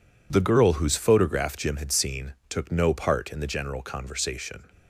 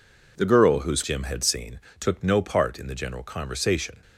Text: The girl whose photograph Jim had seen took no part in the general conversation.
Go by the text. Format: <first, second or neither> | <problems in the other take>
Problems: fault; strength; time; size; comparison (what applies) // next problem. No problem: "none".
first | skips "photograph"; at 1.0 s // pauses between "seen" and "took"; slight; at 1.7 s; 0.22 s long; slight in the first